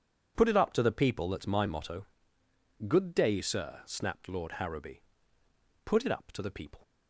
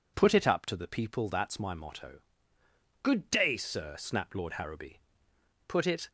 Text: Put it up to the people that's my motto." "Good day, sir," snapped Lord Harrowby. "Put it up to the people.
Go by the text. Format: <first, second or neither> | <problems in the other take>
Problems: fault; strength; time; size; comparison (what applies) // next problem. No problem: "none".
first | stops before "up to the people"; at 6.0 s